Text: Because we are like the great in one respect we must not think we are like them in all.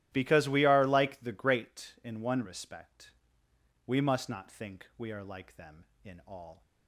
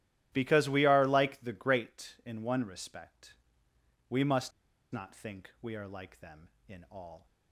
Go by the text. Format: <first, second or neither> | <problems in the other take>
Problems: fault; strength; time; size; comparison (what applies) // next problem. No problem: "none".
first | starts louder than the rest; strong; until 1.3 s; 12.5 dB; strong in the first // pauses between "respect" and "we"; noticeable; at 3.3 s; 0.74 s long; noticeable in the first // pauses between "must" and "not"; at 4.5 s; 0.41 s long